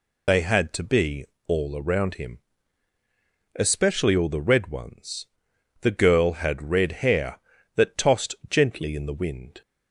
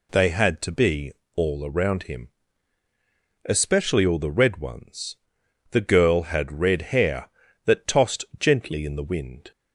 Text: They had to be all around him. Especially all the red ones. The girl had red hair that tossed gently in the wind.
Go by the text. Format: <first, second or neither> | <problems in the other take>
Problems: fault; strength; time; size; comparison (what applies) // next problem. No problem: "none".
second | loses the start of "They"; at 0.2 s; 60 ms // pauses between "be" and "all"; slight; at 1.2 s; 0.22 s long; slight in the second